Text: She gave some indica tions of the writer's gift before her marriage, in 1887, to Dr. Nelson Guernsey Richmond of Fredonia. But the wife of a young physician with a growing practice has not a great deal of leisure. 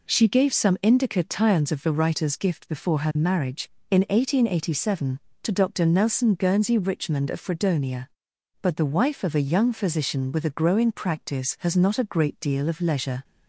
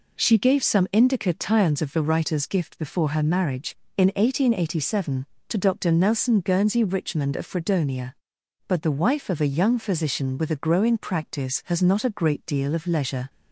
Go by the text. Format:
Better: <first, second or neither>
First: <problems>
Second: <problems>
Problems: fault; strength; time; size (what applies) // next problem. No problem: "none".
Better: neither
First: none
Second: none